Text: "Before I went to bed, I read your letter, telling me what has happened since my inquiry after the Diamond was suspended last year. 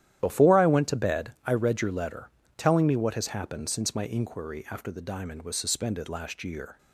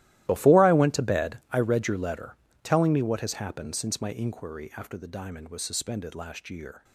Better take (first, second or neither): first